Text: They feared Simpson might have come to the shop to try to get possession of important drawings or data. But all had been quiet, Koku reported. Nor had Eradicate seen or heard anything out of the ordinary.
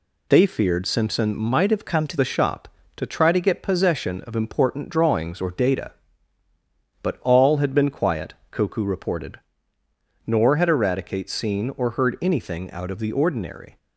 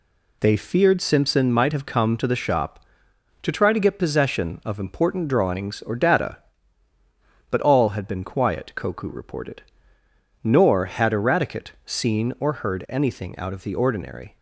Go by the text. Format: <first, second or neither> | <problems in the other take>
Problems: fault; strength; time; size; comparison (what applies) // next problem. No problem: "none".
second | changes voice from "come" to "to"; from 1.8 to 2.1 s; 0.3 s long